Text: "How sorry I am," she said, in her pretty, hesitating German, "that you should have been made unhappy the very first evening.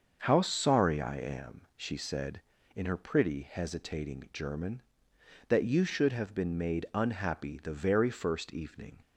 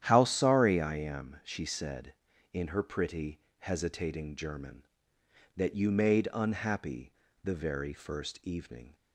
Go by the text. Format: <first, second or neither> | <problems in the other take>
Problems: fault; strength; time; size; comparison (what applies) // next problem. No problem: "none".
first | starts louder than the rest; strong; until 1.0 s; 10.5 dB; also in the first // skips "should have been"; at 5.9 s // pauses between "unhappy" and "the"; slight; at 7.1 s; 0.32 s long